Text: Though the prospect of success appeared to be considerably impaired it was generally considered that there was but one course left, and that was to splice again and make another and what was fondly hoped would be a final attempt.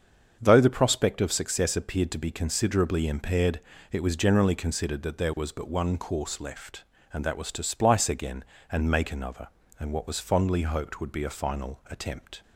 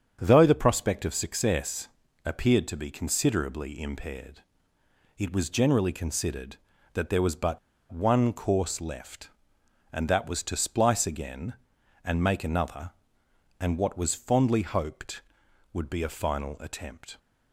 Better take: first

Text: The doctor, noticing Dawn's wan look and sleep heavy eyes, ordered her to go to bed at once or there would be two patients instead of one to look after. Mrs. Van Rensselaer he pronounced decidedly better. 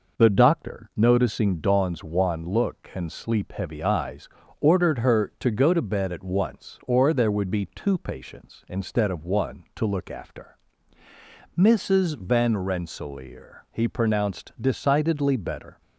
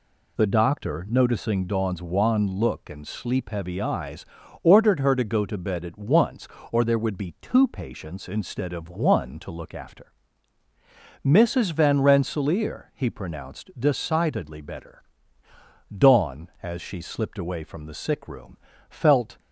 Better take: first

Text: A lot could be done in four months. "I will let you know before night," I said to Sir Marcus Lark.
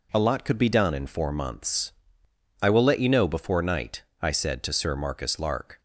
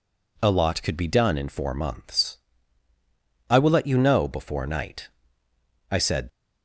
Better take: first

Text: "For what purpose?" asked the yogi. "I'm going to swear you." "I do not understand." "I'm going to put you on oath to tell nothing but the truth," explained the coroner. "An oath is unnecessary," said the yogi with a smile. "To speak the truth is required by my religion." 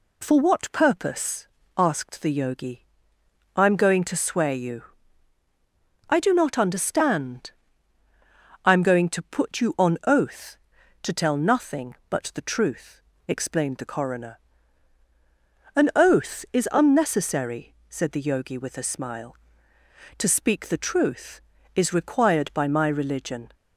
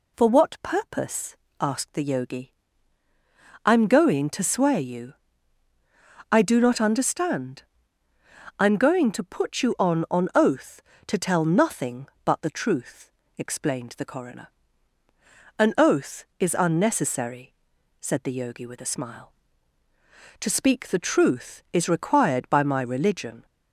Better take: first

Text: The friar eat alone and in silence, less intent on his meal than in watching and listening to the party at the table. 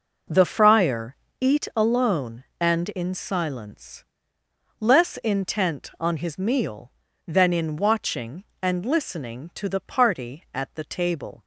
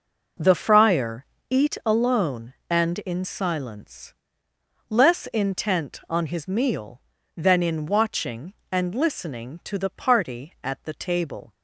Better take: neither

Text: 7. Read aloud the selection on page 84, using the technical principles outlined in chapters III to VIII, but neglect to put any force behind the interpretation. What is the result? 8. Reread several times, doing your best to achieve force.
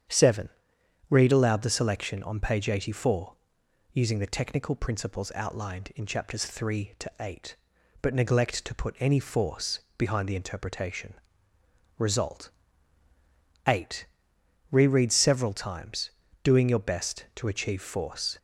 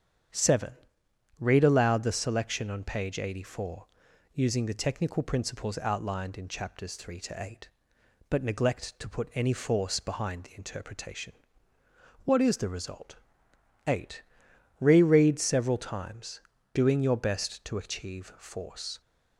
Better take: second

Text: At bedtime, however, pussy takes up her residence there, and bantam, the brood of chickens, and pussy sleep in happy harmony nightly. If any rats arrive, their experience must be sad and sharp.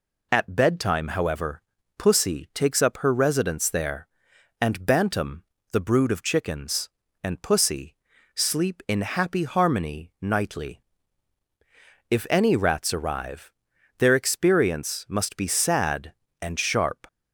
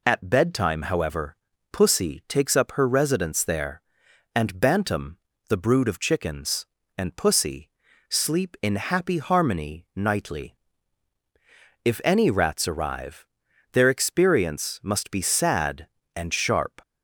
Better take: neither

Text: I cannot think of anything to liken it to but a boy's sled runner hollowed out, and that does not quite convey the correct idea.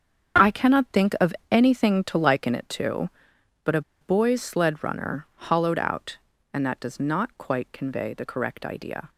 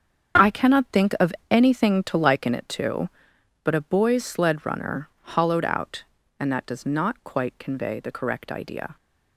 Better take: second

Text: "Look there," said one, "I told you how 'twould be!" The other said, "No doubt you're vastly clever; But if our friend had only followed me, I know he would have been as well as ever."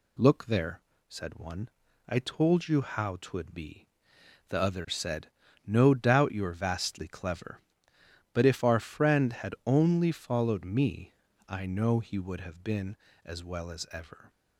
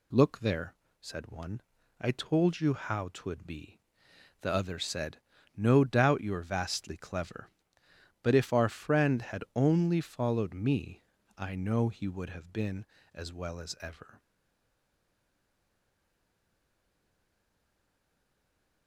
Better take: first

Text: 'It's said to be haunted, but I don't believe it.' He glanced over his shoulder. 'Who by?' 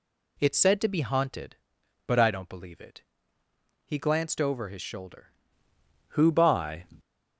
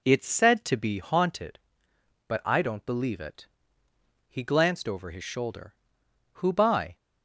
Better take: second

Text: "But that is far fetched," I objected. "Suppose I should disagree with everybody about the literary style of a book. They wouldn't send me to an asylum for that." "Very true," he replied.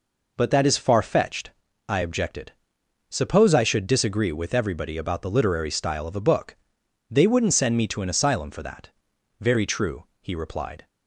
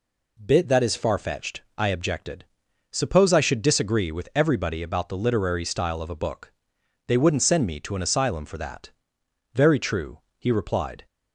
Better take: first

